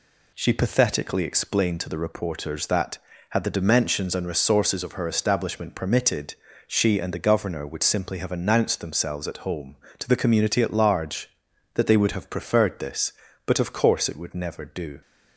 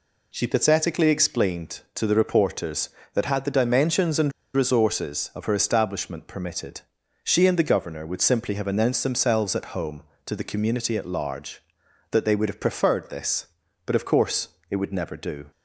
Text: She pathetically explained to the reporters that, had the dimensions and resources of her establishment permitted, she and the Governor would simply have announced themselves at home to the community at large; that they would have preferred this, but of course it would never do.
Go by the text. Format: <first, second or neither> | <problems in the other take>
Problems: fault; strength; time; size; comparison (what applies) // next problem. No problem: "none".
first | pauses between "and" and "resources"; slight; at 4.3 s; 0.22 s long // pauses between "course" and "it"; slight; at 14.4 s; 0.24 s long